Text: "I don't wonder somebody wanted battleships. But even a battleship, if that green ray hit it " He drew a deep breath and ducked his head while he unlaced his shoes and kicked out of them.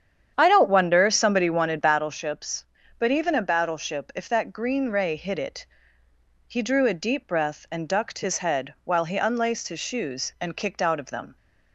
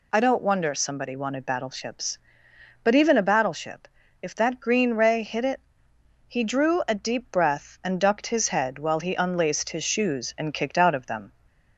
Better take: second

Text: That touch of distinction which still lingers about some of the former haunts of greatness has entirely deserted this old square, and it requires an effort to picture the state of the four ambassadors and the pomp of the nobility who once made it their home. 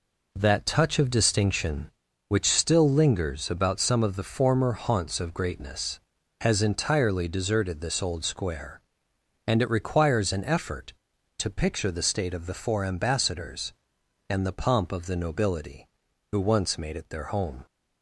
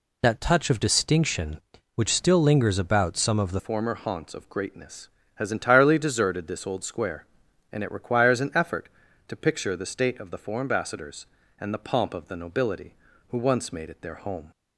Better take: first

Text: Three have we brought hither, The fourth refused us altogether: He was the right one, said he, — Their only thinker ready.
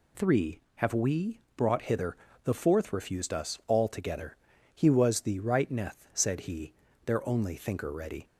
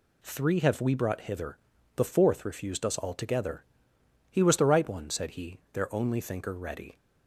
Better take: second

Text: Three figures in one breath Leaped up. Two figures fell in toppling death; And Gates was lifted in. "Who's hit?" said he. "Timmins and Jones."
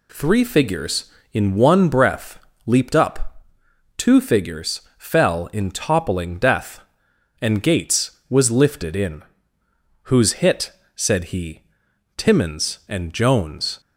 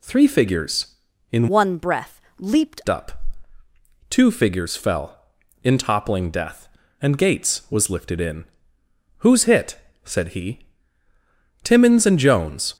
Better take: first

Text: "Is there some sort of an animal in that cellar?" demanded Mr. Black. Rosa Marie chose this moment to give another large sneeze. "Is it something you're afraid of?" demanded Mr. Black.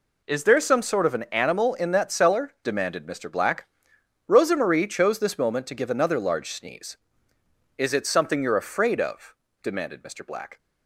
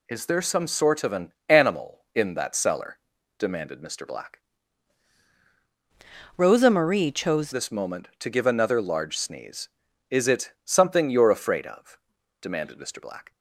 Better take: first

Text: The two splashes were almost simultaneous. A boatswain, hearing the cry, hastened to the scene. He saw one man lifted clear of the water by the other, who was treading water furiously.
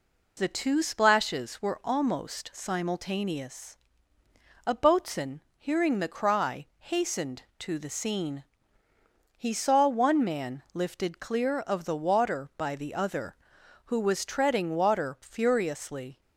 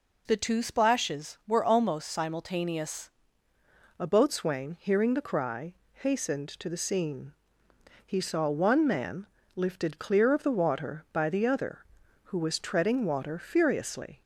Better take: first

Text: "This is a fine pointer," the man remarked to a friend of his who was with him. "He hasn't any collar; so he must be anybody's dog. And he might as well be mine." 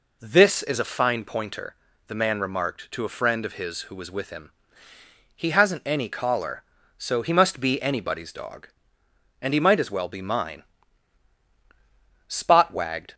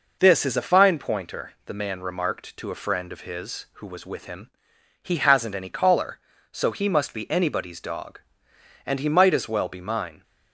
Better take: second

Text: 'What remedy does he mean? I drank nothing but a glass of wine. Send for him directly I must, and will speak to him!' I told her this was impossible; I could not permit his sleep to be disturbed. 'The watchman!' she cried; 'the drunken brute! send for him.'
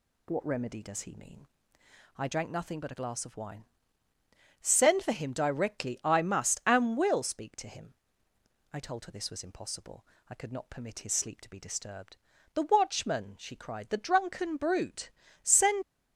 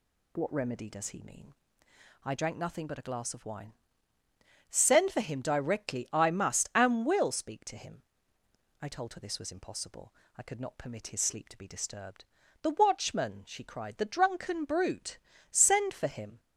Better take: second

